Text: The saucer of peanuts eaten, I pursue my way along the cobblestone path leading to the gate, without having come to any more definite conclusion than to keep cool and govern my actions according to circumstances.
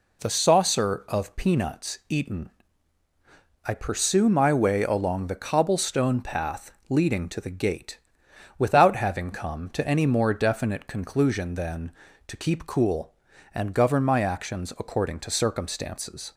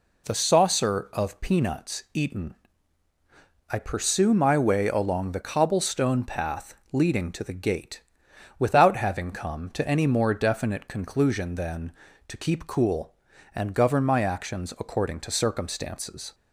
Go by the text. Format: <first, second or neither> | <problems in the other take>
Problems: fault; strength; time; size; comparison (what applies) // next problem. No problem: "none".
neither | pauses between "path" and "leading"; slight; the same in both